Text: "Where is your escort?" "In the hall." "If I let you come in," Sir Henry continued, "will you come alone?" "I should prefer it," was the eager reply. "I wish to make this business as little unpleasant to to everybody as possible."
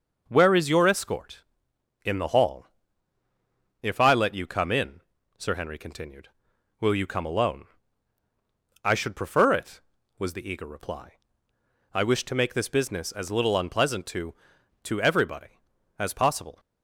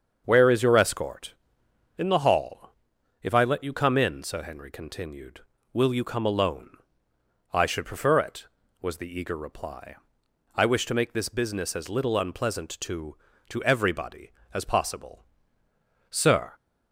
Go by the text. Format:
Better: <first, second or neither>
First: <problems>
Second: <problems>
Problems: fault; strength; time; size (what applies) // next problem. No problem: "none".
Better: first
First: starts louder than the rest; until 1.2 s; 6 dB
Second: starts louder than the rest; until 1.2 s; 7 dB // goes on to say "Sir"; slight; from 16.0 s on; 0.44 s long